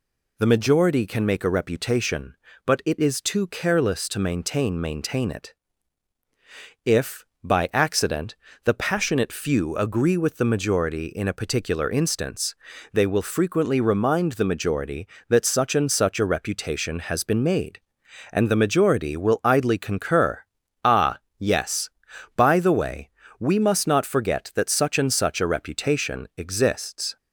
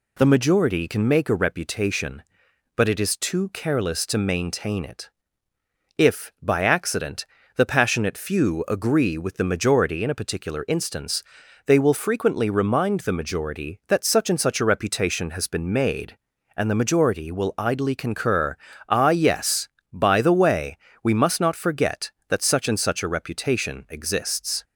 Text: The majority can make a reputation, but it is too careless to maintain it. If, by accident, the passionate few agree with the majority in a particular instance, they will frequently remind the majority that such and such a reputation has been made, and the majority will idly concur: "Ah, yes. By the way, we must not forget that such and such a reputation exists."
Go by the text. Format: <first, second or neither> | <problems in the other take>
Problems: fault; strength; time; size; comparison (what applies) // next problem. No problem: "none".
second | says "maintain" twice; at 4.8 s